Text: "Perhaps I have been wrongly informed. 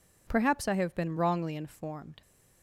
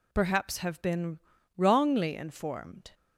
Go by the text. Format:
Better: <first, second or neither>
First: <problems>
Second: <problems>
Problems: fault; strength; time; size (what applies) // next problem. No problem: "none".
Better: first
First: none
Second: skips "I"; at 0.5 s // pauses between "been" and "wrongly"; at 1.1 s; 0.38 s long